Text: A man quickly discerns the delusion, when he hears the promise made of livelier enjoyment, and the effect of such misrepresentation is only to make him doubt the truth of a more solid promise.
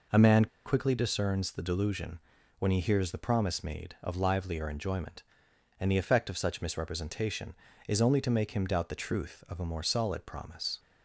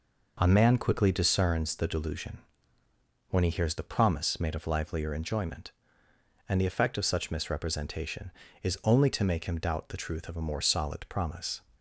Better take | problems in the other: second | pauses between "man" and "quickly"; slight; at 0.4 s; 0.19 s long

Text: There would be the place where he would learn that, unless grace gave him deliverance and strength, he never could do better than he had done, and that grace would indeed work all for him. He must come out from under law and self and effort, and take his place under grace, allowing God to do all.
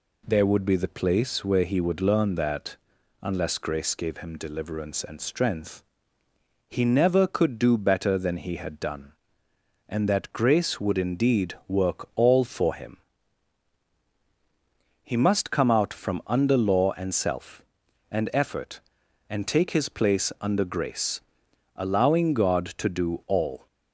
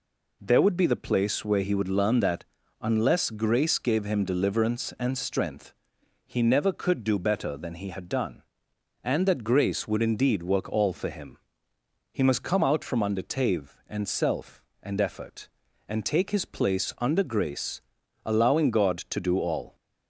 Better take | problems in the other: first | says "tave" for "law"; at 13.2 s

